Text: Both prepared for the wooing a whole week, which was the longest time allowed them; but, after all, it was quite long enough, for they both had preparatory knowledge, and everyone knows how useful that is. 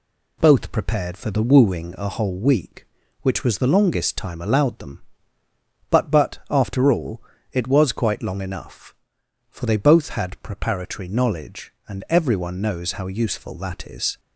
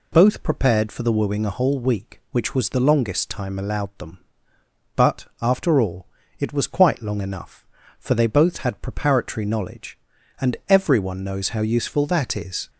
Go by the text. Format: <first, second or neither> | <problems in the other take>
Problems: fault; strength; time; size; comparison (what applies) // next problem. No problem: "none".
second | says "but" twice; at 6.0 s